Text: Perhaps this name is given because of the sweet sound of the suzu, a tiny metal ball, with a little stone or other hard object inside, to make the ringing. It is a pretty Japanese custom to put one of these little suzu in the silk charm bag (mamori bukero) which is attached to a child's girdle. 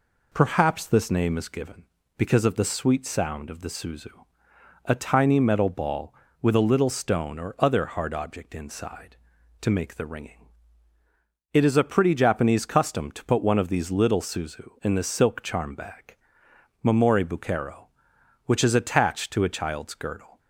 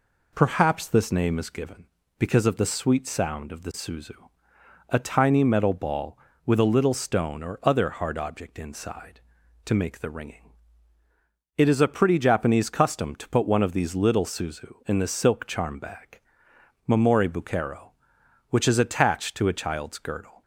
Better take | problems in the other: neither | none

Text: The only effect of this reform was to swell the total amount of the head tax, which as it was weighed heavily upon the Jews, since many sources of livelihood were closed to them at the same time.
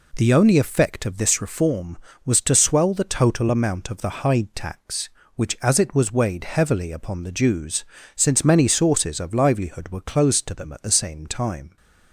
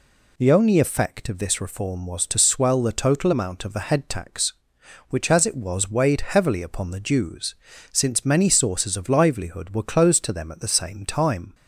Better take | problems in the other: second | says "hide" for "head"; at 4.1 s

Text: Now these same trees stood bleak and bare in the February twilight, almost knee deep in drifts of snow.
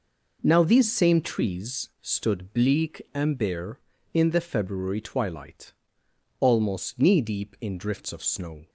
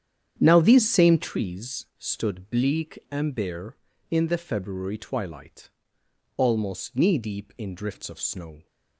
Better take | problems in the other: first | starts louder than the rest; strong; until 1.3 s; 9 dB

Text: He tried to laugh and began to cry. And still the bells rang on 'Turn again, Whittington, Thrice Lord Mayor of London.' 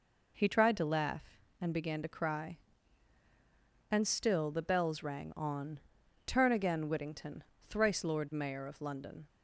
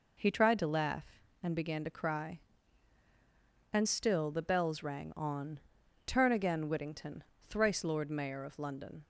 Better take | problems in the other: neither | pauses between "on" and "Turn"; noticeable; the same in both

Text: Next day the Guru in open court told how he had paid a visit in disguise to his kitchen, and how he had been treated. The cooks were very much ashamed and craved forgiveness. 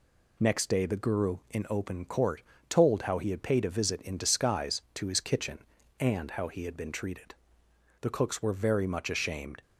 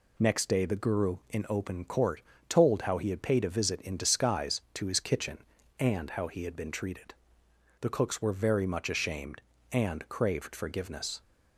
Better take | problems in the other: second | pauses between "court" and "told"; slight; at 2.4 s; 0.28 s long; slight in the second // stops before "and craved forgiveness"; at 9.6 s

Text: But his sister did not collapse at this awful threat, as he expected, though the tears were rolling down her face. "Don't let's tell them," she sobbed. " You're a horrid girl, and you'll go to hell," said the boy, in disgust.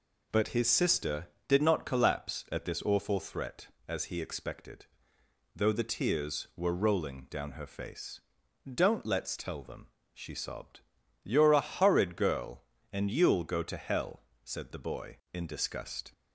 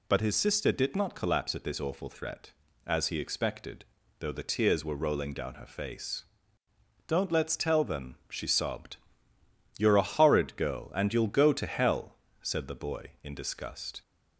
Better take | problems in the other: neither | none

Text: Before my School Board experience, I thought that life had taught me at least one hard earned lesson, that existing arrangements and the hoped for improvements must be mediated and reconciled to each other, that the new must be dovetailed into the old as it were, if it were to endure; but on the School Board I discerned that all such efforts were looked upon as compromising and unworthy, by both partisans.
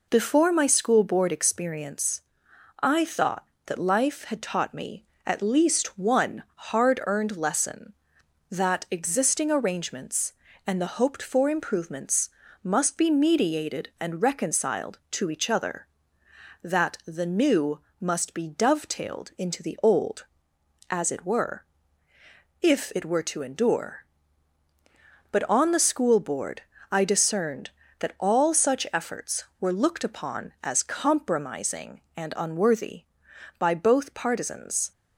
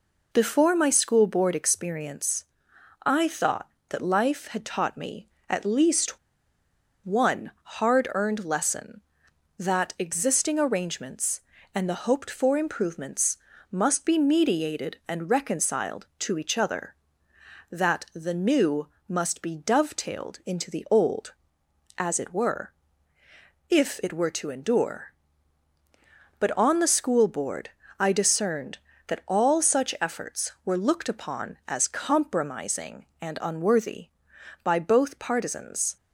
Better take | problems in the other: first | pauses between "least" and "one"; noticeable; at 6.1 s; 0.87 s long // pauses between "improvements" and "must"; slight; at 13.3 s; 0.34 s long; slight in the first // pauses between "new" and "must"; slight; at 18.8 s; 0.20 s long; slight in the first // pauses between "Board" and "I"; slight; at 27.7 s; 0.28 s long; slight in the first

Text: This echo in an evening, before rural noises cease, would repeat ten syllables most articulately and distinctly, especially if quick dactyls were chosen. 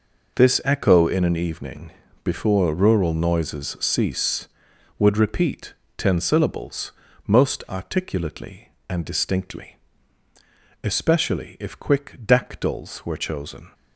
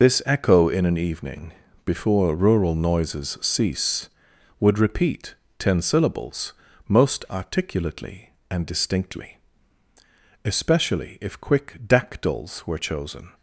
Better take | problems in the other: first | loses the start of "This"; at 0.0 s; 40 ms // pauses between "repeat" and "ten"; slight; at 5.3 s; 0.22 s long; slight in the first // pauses between "syllables" and "most"; slight; at 6.5 s; 0.36 s long; slight in the first

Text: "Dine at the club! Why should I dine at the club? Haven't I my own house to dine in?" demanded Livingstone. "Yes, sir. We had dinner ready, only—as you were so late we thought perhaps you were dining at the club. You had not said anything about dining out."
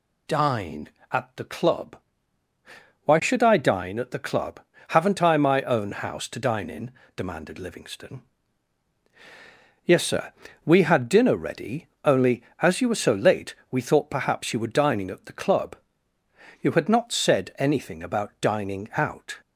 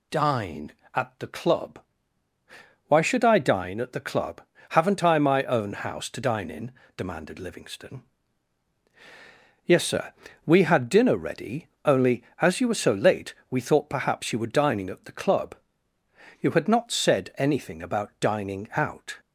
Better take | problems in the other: neither | pauses between "late" and "we"; slight; the same in both

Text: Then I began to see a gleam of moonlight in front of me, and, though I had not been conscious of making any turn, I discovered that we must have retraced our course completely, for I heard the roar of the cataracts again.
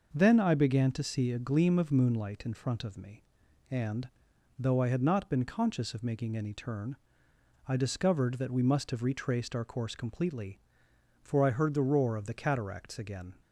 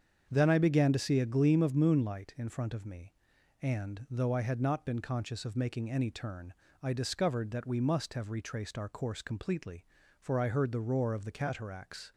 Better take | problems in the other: first | starts louder than the rest; strong; until 1.3 s; 7.5 dB // stops before "again"; at 12.1 s

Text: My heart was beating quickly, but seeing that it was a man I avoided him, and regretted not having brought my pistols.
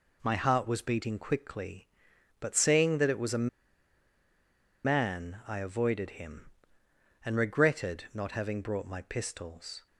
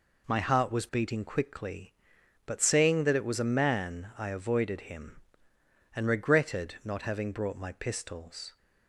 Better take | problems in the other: second | pauses between "a" and "man"; strong; at 3.4 s; 1.3 s long

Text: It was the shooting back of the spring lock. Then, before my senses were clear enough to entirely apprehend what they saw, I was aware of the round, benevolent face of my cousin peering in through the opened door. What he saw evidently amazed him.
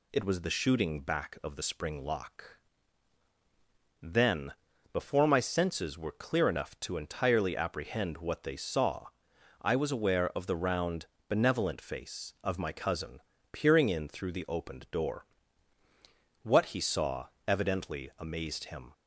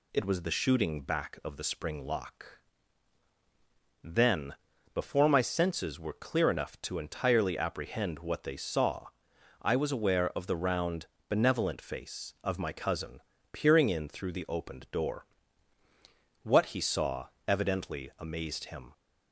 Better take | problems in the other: neither | pauses between "cousin" and "peering"; slight; the same in both // pauses between "saw" and "evidently"; slight; the same in both

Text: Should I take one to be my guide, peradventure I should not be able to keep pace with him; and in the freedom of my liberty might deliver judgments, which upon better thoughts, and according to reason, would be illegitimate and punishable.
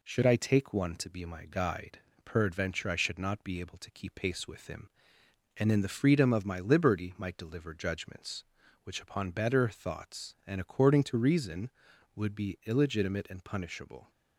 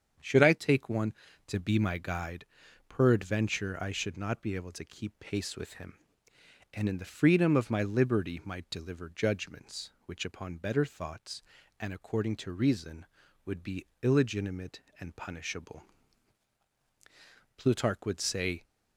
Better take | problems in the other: first | starts louder than the rest; strong; until 1.5 s; 7.5 dB // pauses between "be" and "illegitimate"; slight; at 13.8 s; 0.16 s long // goes on to say "Plutarch would say"; noticeable; from 17.5 s on; 1.0 s long

